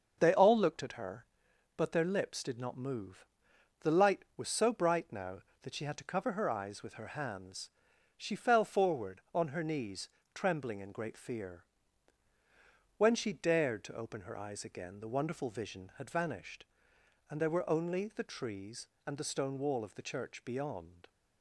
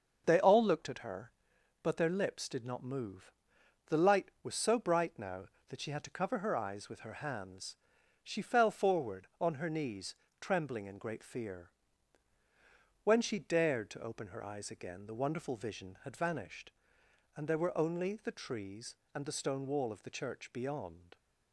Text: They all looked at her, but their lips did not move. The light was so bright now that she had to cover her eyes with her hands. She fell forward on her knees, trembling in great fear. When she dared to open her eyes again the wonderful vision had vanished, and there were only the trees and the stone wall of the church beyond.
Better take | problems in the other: neither | starts louder than the rest; the same in both

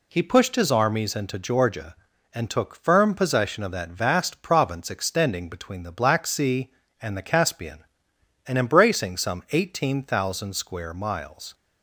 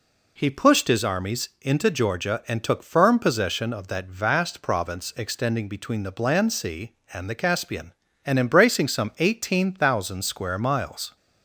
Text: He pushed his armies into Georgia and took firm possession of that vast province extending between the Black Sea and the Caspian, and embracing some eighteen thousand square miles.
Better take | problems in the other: first | says "Bland" for "Black"; at 6.1 s

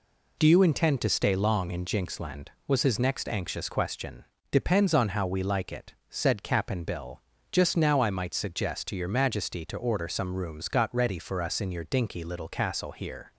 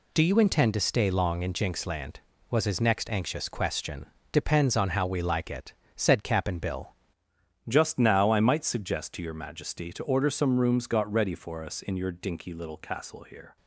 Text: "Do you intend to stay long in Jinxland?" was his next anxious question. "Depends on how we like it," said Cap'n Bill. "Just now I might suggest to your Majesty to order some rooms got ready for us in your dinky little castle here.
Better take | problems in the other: first | changes voice at "Just"; from 7.6 s on; 5.9 s long

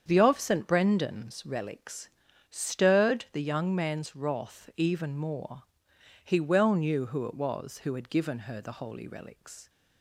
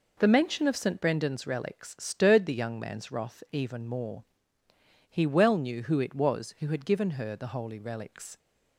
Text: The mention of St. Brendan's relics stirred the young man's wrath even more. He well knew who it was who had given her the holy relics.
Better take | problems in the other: second | starts louder than the rest; strong; until 1.0 s; 7.5 dB // skips "mention"; at 0.2 s // pauses between "relics" and "stirred"; at 2.0 s; 0.42 s long

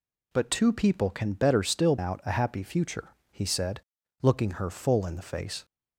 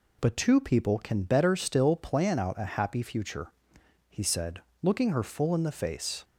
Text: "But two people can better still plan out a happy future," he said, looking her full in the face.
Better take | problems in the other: second | skips "plan"; at 1.9 s

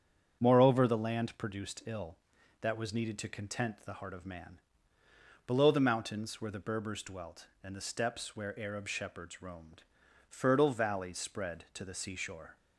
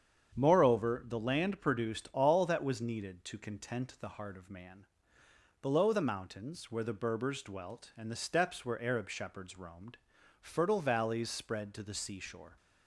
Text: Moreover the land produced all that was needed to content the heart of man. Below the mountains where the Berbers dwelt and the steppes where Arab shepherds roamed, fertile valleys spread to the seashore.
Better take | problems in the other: second | starts louder than the rest; strong; until 1.4 s; 8 dB; strong in the second // says "ill" for "all"; at 1.8 s

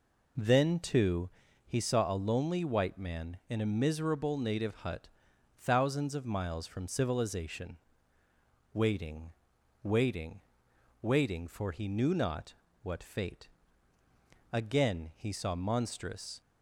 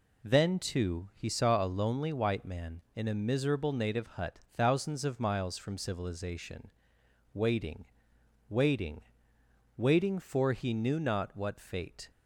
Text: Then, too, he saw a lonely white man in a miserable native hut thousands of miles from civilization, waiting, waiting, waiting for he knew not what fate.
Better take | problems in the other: second | pauses between "hut" and "thousands"; noticeable; at 5.0 s; 0.48 s long; slight in the second // pauses between "not" and "what"; slight; at 12.5 s; 0.30 s long // goes on to say "Again he saw monstrous"; strong; from 14.5 s on; 1.8 s long

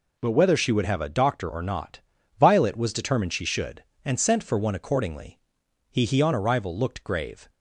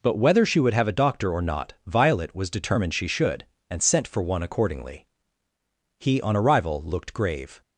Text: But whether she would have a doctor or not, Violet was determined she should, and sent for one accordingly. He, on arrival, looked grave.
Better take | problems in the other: second | says "He" twice; at 6.0 s

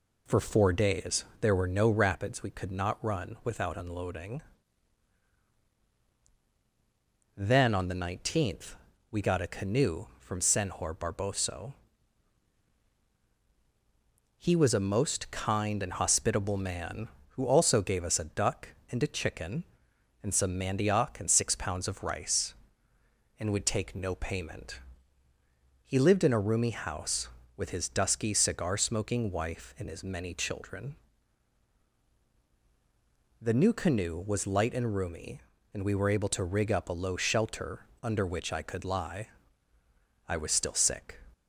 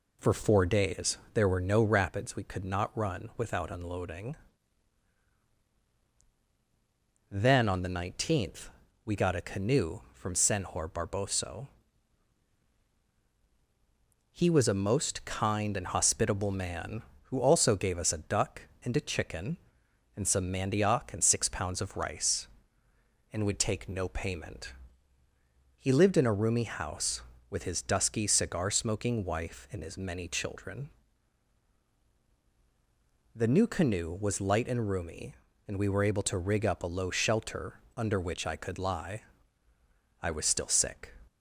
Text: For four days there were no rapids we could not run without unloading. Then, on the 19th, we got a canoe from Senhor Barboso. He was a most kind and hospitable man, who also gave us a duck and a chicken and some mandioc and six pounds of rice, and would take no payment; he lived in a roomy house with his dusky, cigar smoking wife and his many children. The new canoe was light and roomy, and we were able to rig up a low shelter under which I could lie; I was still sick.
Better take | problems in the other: neither | pauses between "days" and "there"; slight; the same in both // pauses between "shelter" and "under"; slight; the same in both

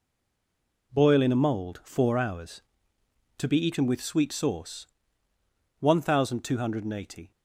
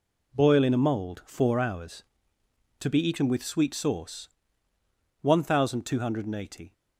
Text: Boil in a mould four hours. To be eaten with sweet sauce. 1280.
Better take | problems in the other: second | stays silent before the first word; slight; until 0.9 s; 0.9 s long

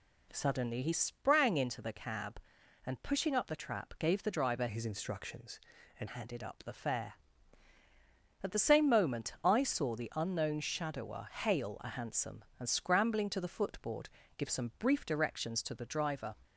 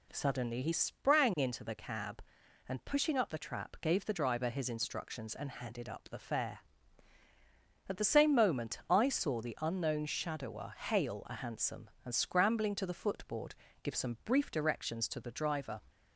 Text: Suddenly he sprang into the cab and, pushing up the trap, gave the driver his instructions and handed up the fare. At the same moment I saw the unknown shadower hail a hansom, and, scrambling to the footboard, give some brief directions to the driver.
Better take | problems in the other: second | changes voice from "his" to "and"; from 4.6 to 6.0 s; 1.4 s long

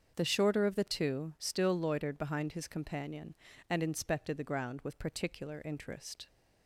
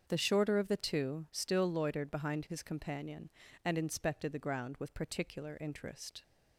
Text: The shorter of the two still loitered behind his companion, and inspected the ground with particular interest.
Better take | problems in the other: neither | starts louder than the rest; the same in both

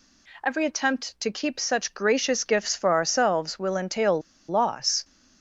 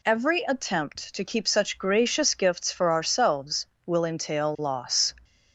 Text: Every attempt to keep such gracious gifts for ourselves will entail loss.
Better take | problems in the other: second | pauses between "entail" and "loss"; slight; at 4.2 s; 0.28 s long

